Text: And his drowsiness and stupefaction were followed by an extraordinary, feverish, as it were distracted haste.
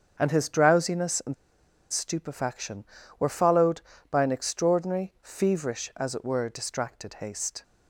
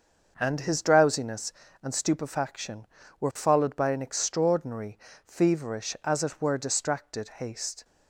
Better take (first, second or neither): second